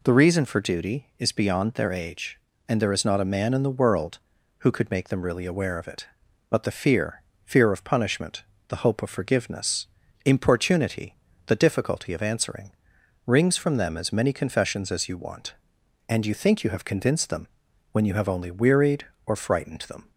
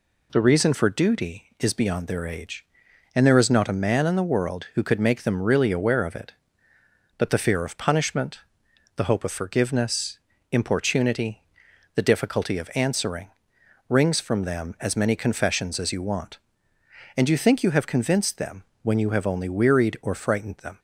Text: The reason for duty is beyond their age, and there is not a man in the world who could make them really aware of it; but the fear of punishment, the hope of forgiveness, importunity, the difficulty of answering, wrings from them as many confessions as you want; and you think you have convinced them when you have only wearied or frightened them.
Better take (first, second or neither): second